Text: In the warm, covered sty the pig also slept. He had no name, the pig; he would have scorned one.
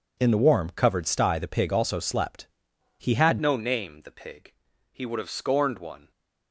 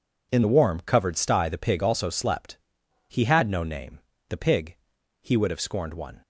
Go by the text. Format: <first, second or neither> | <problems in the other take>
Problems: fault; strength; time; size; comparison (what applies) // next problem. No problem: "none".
second | changes voice at "no"; from 3.4 s on; 2.7 s long